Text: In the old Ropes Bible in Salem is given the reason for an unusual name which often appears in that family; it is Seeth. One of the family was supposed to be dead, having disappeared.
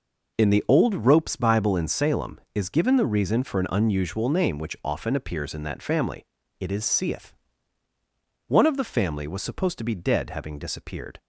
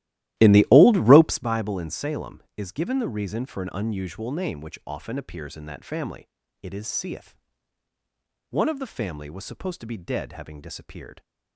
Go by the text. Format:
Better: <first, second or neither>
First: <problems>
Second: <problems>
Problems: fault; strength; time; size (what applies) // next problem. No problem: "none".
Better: first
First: none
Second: starts louder than the rest; strong; until 1.5 s; 15 dB